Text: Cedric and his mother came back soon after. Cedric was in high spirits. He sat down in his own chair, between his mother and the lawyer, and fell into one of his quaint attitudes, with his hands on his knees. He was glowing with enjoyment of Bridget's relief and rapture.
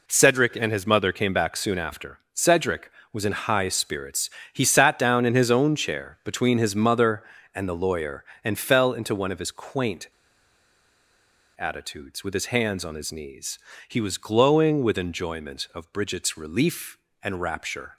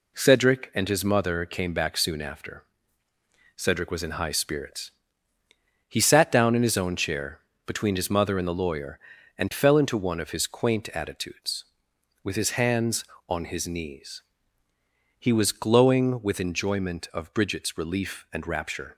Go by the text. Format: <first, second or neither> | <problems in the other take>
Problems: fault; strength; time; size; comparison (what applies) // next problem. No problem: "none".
second | pauses between "quaint" and "attitudes"; strong; at 10.0 s; 1.5 s long